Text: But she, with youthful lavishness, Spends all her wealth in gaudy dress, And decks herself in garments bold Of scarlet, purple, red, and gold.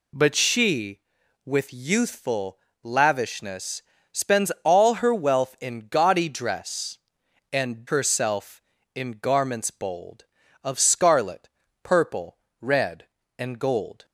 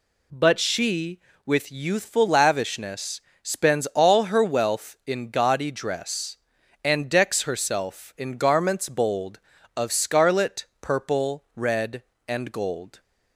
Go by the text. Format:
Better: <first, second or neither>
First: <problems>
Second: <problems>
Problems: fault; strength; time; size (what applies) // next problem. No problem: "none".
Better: second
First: pauses between "youthful" and "lavishness"; slight; at 2.5 s; 0.24 s long // skips "decks"; at 7.8 s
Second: none